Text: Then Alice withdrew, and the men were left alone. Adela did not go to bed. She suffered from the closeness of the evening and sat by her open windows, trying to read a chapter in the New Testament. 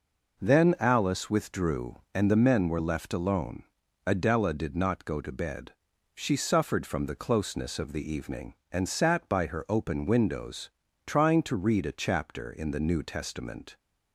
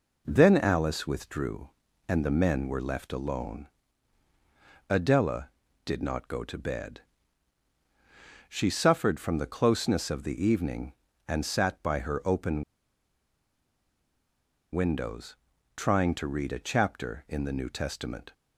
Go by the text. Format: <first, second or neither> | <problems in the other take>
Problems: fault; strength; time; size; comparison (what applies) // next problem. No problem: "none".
first | pauses between "open" and "windows"; strong; at 12.6 s; 2.0 s long